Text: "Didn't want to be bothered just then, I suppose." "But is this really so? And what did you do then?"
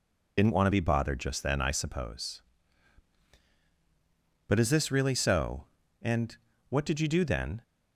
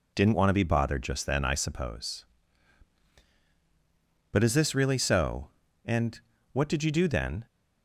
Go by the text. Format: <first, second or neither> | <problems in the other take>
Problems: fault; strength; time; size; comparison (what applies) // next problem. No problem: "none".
second | loses the start of "Didn't"; at 0.3 s; 50 ms // pauses between "And" and "what"; slight; at 6.3 s; 0.34 s long; slight in the second